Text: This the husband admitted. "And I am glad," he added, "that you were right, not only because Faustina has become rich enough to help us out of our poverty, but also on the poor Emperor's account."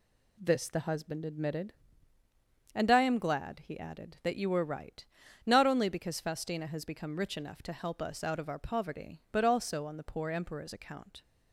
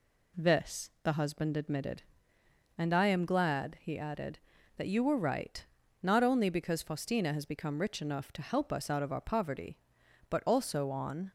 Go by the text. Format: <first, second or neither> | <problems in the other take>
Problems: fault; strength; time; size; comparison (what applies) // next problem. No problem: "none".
first | stops before "the poor Emperor's account"; at 11.2 s